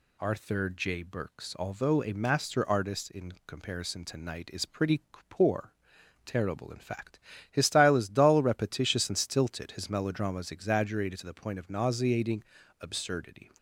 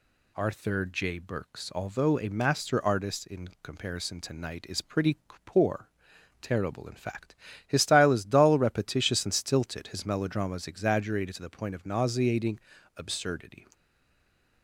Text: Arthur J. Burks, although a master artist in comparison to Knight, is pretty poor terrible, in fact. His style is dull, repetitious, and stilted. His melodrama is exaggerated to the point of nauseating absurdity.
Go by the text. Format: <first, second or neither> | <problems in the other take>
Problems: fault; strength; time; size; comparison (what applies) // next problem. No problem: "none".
first | pauses between "pretty" and "poor"; slight; at 5.1 s; 0.28 s long; slight in the first // pauses between "poor" and "terrible"; noticeable; at 5.8 s; 0.52 s long; noticeable in the first // pauses between "nauseating" and "absurdity"; at 12.5 s; 0.38 s long; also in the first // stays silent after the last word; slight; from 13.7 s on; 0.9 s long